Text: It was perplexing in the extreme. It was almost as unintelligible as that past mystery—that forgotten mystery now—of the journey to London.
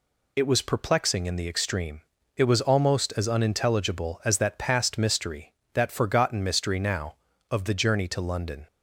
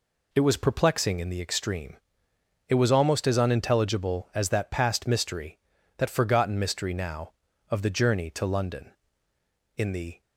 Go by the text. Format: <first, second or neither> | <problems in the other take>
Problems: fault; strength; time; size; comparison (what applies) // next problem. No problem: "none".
first | goes on to say "In the"; slight; from 9.7 s on; 0.46 s long